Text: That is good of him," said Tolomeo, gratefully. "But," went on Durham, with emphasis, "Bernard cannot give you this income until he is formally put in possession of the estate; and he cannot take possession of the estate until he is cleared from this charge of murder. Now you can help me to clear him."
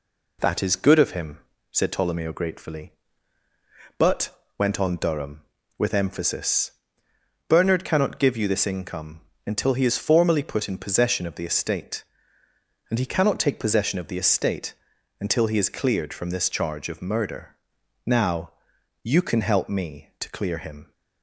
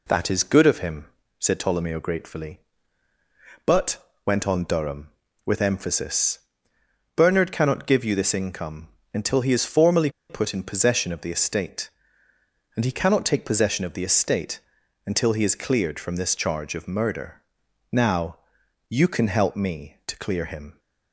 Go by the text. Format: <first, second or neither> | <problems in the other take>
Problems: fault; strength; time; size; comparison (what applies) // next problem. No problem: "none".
first | pauses between "income" and "until"; slight; at 8.8 s; 0.26 s long; slight in the first // pauses between "formally" and "put"; slight; at 10.0 s; 0.20 s long // pauses between "estate" and "until"; noticeable; at 14.5 s; 0.46 s long; noticeable in the first // pauses between "Now" and "you"; noticeable; at 18.3 s; 0.52 s long; noticeable in the first